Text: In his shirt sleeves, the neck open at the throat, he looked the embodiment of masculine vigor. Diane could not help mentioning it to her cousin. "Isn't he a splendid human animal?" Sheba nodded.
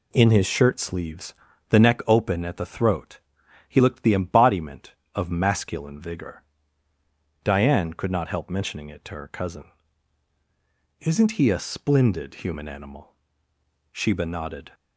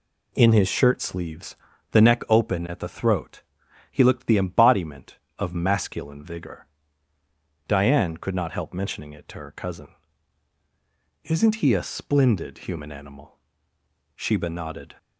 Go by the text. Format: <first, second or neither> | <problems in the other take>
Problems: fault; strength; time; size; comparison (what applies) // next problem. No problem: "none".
neither | none